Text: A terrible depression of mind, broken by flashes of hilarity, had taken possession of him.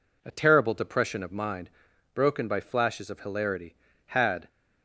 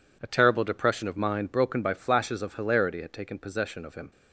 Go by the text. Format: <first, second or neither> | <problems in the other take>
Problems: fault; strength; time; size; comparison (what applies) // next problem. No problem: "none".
second | stops before "taken possession of him"; at 4.4 s